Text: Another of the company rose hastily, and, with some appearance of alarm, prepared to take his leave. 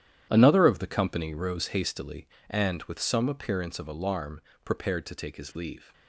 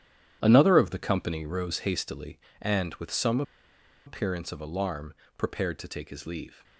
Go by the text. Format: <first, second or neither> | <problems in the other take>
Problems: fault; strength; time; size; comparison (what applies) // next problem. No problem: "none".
first | starts louder than the rest; strong; until 1.4 s; 10.5 dB; strong in the first // pauses between "some" and "appearance"; noticeable; at 3.4 s; 0.64 s long